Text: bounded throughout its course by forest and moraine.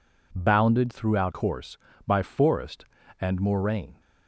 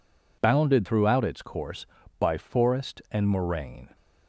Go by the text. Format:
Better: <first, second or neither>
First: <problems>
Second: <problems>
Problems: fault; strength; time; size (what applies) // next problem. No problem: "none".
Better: second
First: skips "its"; at 1.3 s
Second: none